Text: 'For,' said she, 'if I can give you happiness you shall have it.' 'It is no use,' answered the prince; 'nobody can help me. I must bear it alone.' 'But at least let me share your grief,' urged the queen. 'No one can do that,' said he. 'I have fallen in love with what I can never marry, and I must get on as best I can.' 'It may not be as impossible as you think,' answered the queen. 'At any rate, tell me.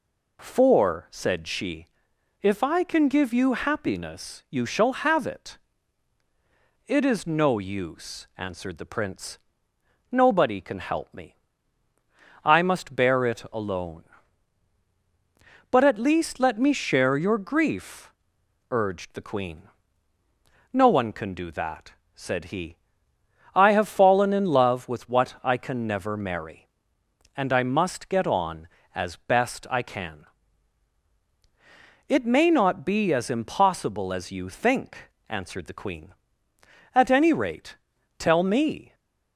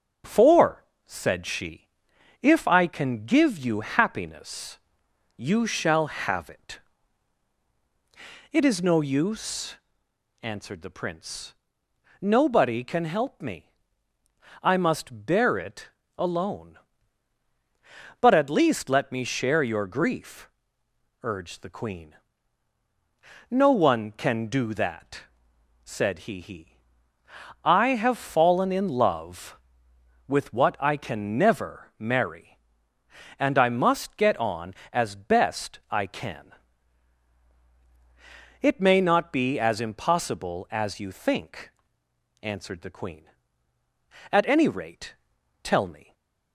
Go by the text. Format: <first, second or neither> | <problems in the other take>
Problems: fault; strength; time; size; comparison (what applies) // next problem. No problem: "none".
first | starts louder than the rest; until 1.4 s; 6.5 dB // pauses between "happiness" and "you"; noticeable; at 4.7 s; 0.58 s long // pauses between "it" and "alone"; slight; at 15.8 s; 0.28 s long // says "he" twice; at 26.3 s // stays silent after the last word; slight; from 46.0 s on; 0.5 s long